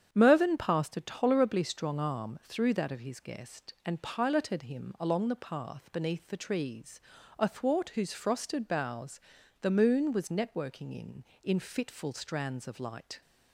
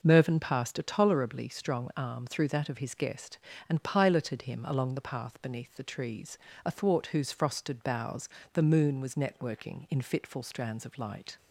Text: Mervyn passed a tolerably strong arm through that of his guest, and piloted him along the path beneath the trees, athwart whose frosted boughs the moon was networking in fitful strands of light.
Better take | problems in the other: second | starts louder than the rest; strong; until 1.1 s; 8.5 dB // pauses between "boughs" and "the"; at 9.2 s; 0.40 s long; slight in the second // says "in" twice; at 11.4 s

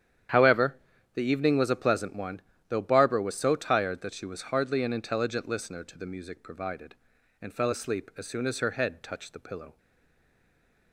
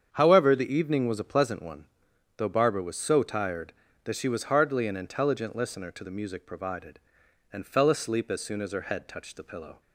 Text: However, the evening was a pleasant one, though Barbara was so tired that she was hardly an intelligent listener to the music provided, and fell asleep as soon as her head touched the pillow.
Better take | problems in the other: second | starts louder than the rest; strong; until 1.6 s; 9.5 dB; strong in the second // stays silent after the last word; noticeable; from 9.7 s on; 1.2 s long

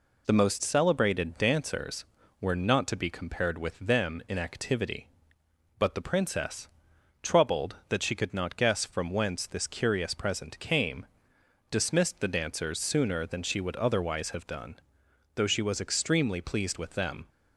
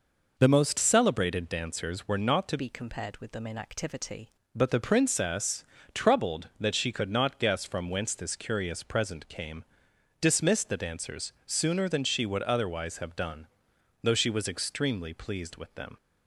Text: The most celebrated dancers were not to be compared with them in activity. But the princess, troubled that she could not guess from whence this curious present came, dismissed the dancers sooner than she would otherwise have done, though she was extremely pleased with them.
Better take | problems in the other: first | changes voice from "be" to "activity"; from 2.5 to 4.2 s; 1.7 s long

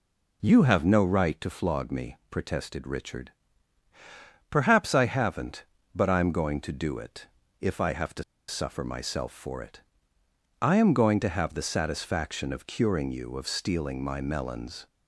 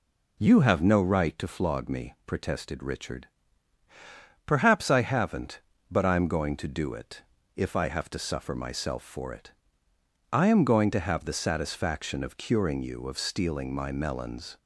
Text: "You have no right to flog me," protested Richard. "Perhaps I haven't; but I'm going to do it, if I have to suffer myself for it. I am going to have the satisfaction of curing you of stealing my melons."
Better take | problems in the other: second | pauses between "to" and "suffer"; slight; at 8.2 s; 0.24 s long

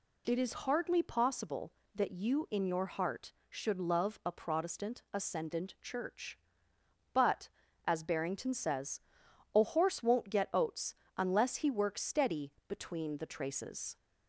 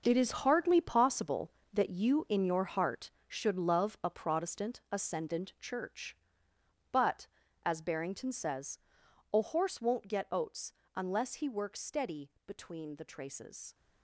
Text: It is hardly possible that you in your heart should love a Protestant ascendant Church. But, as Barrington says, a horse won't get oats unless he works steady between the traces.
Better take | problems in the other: first | gets quieter; strong; throughout; 11.5 dB // pauses between "oats" and "unless"; slight; at 10.7 s; 0.20 s long; slight in the first // pauses between "steady" and "between"; slight; at 12.2 s; 0.18 s long; slight in the first

